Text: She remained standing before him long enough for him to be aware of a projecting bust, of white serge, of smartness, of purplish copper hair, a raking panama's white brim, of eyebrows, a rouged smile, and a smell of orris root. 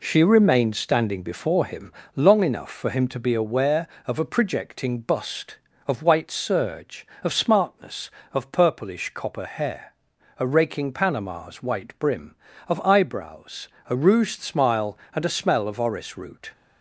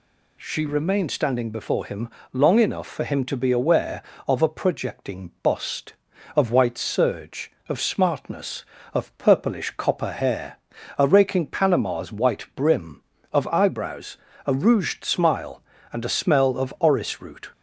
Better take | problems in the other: second | gets quieter; noticeable; throughout; 4.5 dB // pauses between "him" and "long"; slight; at 1.9 s; 0.22 s long; slight in the second

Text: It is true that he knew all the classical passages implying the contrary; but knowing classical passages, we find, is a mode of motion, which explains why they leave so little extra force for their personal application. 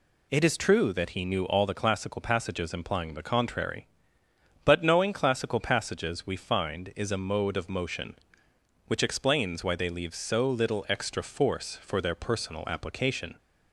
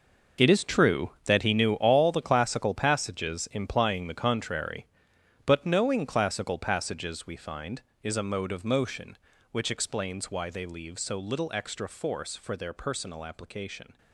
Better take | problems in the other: first | gets quieter; strong; throughout; 13.5 dB

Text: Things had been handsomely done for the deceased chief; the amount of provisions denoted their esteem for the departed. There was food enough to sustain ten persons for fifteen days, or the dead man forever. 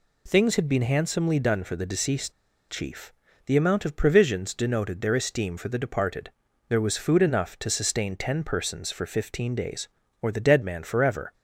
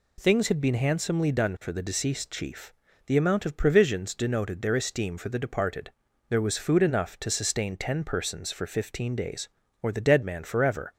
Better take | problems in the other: second | pauses between "deceased" and "chief"; at 2.3 s; 0.38 s long

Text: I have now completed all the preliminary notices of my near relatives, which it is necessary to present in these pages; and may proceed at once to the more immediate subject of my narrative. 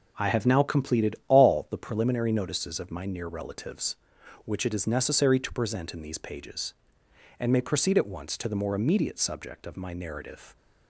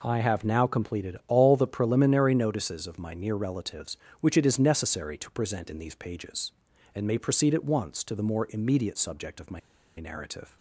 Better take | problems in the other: first | pauses between "my" and "narrative"; at 9.5 s; 0.38 s long

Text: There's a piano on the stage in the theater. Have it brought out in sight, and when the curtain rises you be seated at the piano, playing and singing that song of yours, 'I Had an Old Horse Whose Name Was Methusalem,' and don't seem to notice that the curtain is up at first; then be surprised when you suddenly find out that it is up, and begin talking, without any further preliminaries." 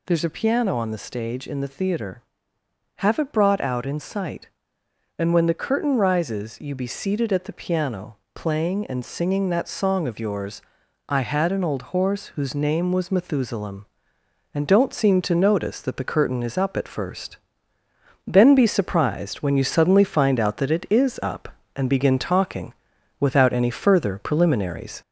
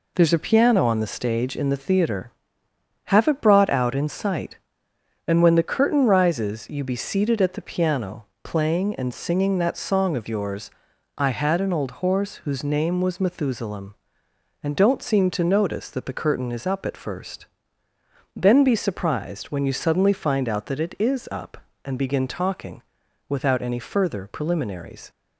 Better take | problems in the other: second | gets louder; slight; throughout; 3 dB

